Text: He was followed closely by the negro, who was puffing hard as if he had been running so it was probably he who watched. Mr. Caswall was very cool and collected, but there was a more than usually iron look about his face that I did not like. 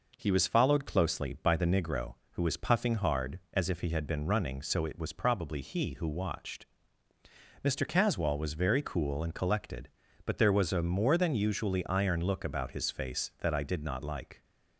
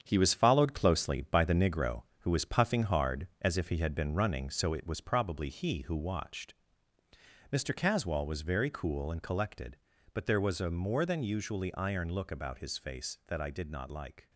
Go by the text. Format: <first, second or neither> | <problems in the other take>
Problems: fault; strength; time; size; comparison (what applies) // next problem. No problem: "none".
first | gets quieter; throughout; 6.5 dB